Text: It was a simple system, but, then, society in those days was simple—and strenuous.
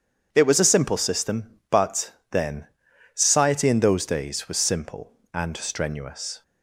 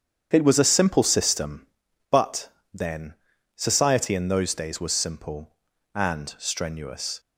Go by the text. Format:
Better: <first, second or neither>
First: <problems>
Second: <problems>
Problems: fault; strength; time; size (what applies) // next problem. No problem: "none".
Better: neither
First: starts louder than the rest; strong; until 1.3 s; 8 dB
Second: starts louder than the rest; strong; until 1.3 s; 8.5 dB